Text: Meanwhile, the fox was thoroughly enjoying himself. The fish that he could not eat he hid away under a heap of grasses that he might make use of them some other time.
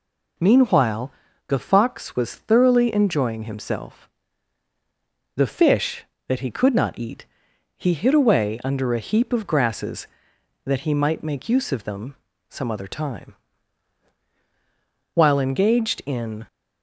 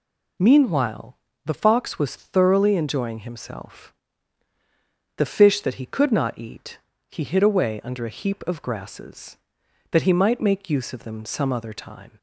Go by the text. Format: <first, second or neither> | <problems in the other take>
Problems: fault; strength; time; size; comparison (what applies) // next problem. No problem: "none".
second | pauses between "eat" and "he"; noticeable; at 7.2 s; 0.52 s long; slight in the second // pauses between "them" and "some"; slight; at 12.1 s; 0.34 s long // goes on to say "While engaged in"; from 15.1 s on; 1.3 s long